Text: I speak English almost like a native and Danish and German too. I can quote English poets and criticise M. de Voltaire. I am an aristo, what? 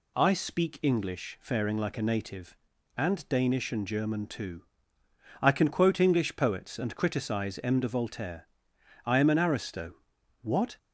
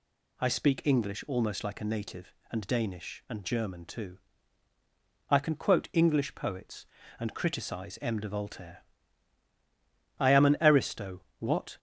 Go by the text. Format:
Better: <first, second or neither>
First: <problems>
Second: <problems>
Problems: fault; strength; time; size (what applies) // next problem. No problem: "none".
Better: second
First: says "faring" for "almost"; at 1.4 s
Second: none